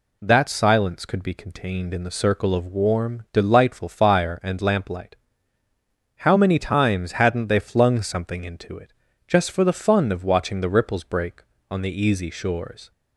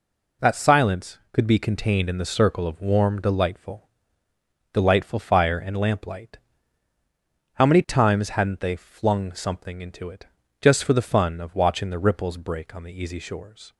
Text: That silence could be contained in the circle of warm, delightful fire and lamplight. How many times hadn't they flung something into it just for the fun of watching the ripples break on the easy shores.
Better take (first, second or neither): first